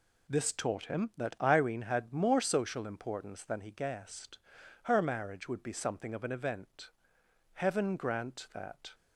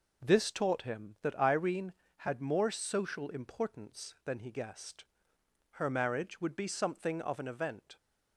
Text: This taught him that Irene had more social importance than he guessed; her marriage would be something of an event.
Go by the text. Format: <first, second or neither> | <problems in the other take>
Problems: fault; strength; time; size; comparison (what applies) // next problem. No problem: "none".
second | goes on to say "Heaven grant that"; from 7.5 s on; 1.4 s long